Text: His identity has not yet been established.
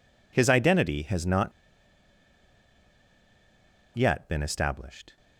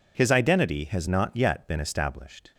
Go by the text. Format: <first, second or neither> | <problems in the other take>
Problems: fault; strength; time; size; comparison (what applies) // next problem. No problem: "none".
second | pauses between "not" and "yet"; strong; at 1.5 s; 2.4 s long